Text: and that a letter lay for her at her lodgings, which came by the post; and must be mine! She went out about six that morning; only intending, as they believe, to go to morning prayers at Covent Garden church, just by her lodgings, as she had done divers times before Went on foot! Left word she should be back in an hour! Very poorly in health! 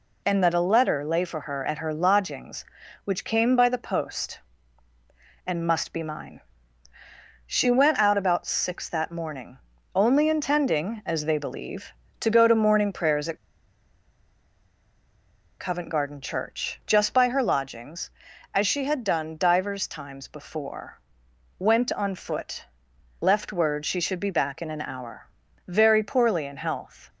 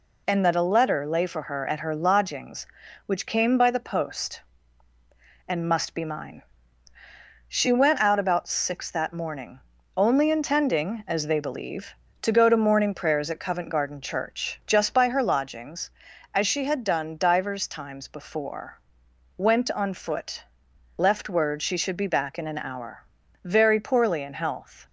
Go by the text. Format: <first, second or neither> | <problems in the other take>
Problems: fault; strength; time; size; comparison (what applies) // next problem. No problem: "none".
second | pauses between "at" and "Covent"; strong; at 13.3 s; 2.2 s long // pauses between "before" and "Went"; noticeable; at 20.9 s; 0.60 s long; noticeable in the second